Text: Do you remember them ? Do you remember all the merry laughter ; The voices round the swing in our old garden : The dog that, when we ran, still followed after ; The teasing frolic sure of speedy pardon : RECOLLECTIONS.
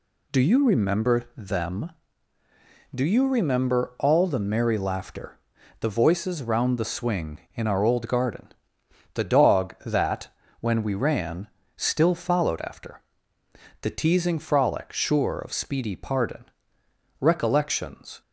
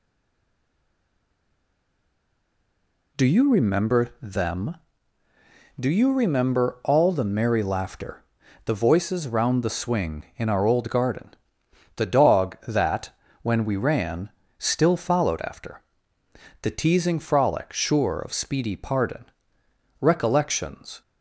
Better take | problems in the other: first | stays silent before the first word; strong; until 3.1 s; 3.1 s long

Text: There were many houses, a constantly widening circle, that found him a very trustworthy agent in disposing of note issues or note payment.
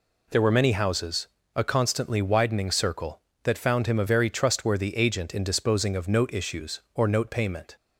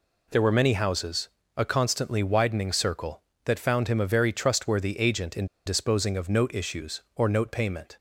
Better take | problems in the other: first | pauses between "in" and "disposing"; slight; at 5.4 s; 0.20 s long

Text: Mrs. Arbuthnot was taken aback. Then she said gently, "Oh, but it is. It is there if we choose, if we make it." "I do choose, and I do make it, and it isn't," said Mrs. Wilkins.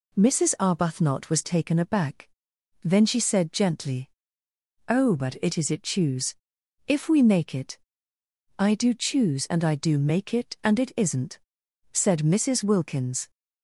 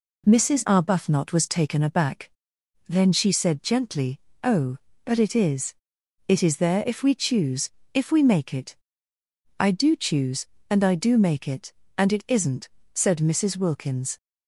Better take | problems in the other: second | skips "is there if we"; at 5.8 s

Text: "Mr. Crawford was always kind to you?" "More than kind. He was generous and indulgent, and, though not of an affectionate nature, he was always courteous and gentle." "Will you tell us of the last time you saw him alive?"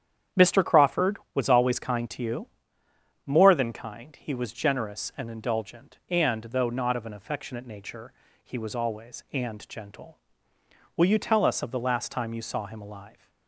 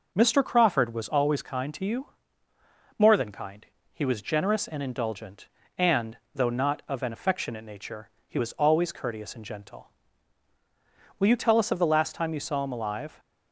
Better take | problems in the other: second | starts louder than the rest; strong; until 1.5 s; 9 dB // skips "courteous"; at 9.2 s

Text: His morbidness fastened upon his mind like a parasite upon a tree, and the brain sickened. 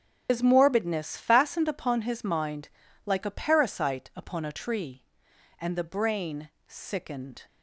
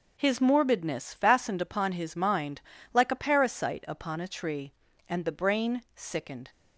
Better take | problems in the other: second | loses the start of "His"; at 0.2 s; 90 ms // starts louder than the rest; strong; until 1.3 s; 8.5 dB // pauses between "mind" and "like"; at 2.6 s; 0.38 s long; slight in the second // pauses between "brain" and "sickened"; slight; at 6.5 s; 0.16 s long

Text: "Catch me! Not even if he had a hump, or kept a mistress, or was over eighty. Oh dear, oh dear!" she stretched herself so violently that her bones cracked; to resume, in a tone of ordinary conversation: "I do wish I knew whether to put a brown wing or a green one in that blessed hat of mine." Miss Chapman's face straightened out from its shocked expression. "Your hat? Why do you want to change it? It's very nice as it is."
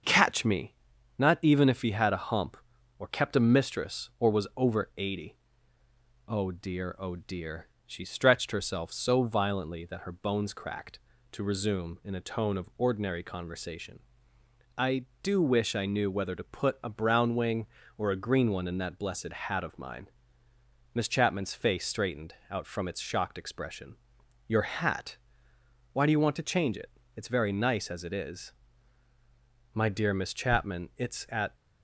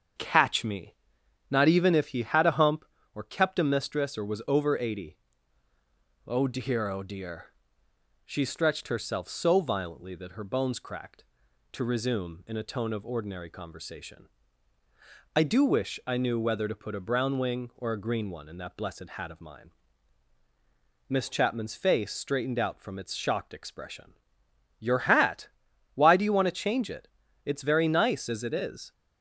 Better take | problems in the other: second | starts louder than the rest; until 1.5 s; 7 dB; strong in the second // pauses between "straightened" and "out"; slight; at 22.3 s; 0.16 s long // goes on to say "My dear Miss Chapman it's at"; strong; from 29.7 s on; 1.8 s long

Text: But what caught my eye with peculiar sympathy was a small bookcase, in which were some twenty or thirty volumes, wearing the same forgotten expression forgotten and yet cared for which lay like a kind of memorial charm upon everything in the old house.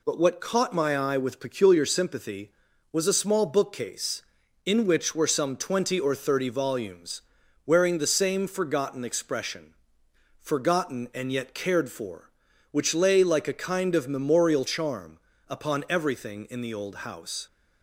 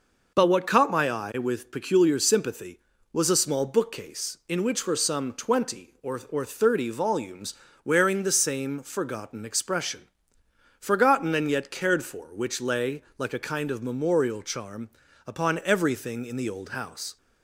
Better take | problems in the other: first | says "or" twice; at 6.2 s // pauses between "expression" and "forgotten"; noticeable; at 10.0 s; 0.78 s long; noticeable in the first // pauses between "lay" and "like"; slight; at 13.0 s; 0.16 s long // pauses between "charm" and "upon"; at 14.8 s; 0.38 s long; slight in the first

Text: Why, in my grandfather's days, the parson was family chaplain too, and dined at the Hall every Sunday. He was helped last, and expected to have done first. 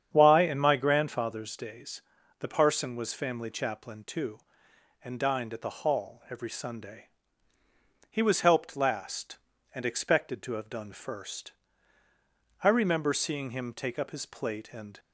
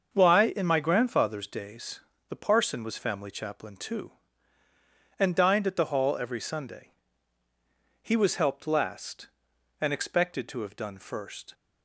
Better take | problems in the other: second | starts louder than the rest; strong; until 1.1 s; 8.5 dB; also in the second // goes on to say "I remember seeing him take up his plate and"; strong; from 12.6 s on; 2.3 s long

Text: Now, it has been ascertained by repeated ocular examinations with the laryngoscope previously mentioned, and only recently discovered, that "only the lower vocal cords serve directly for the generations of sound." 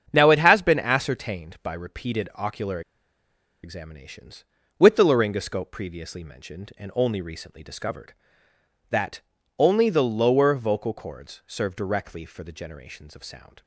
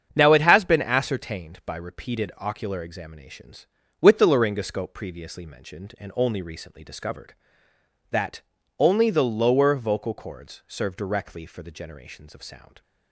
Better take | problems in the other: second | starts louder than the rest; strong; until 1.1 s; 7.5 dB; strong in the second // pauses between "ocular" and "examinations"; noticeable; at 2.8 s; 0.83 s long // pauses between "that" and "only"; slight; at 9.2 s; 0.36 s long; slight in the second

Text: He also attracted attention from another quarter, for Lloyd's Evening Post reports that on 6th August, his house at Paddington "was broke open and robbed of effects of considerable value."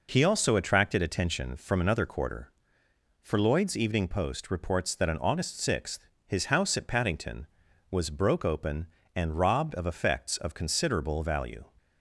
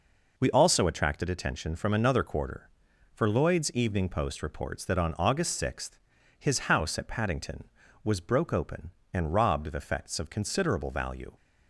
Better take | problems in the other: first | says "We" for "He"; at 0.3 s

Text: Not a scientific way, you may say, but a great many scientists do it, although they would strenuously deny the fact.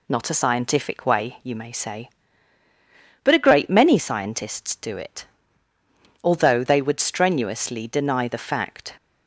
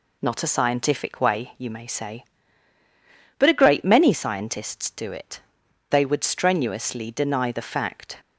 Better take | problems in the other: first | skips "although"; at 5.6 s

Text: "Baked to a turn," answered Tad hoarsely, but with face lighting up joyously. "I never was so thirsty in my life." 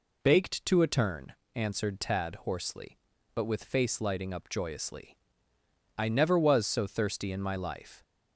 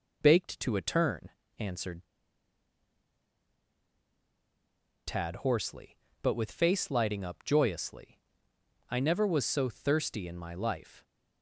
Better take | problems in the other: first | pauses between "answered" and "Tad"; strong; at 2.0 s; 3.0 s long

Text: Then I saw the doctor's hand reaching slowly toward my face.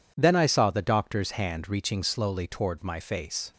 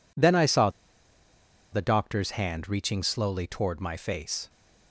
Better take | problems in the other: first | pauses between "saw" and "the"; at 0.6 s; 1.0 s long

